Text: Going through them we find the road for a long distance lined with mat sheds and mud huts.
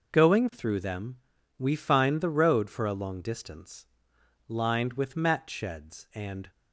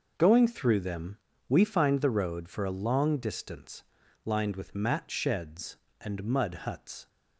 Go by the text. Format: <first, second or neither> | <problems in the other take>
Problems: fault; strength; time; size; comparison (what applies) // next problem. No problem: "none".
second | pauses between "them" and "we"; at 1.1 s; 0.42 s long; slight in the second // pauses between "distance" and "lined"; noticeable; at 3.8 s; 0.62 s long; also in the second // stops before "mud huts"; at 6.5 s